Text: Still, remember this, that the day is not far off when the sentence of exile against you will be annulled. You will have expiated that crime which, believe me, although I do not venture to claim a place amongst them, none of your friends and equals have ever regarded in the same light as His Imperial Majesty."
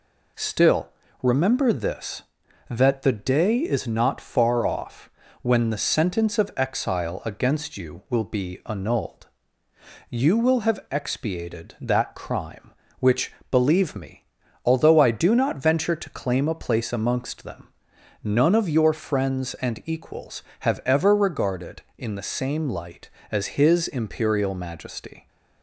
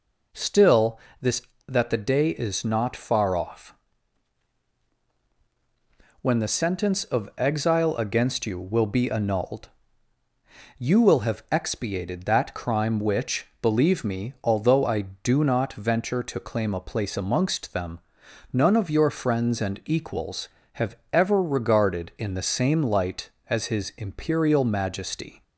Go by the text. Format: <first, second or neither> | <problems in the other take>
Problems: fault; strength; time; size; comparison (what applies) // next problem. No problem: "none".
first | skips "remember"; at 1.0 s // pauses between "off" and "when"; strong; at 3.7 s; 2.4 s long; slight in the first // pauses between "have" and "ever"; slight; at 20.9 s; 0.18 s long